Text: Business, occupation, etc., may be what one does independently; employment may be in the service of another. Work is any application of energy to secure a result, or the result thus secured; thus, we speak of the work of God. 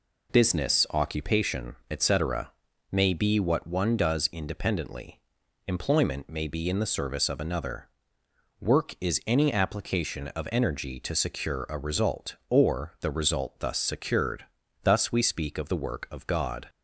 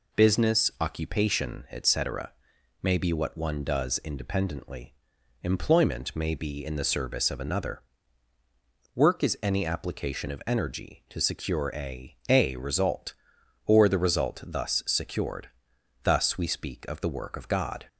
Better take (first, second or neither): first